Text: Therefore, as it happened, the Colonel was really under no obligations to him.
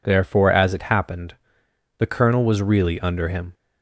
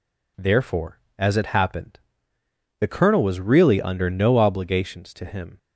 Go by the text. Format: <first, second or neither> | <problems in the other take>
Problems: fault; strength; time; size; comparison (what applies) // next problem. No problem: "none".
second | skips "no obligations to"; at 3.2 s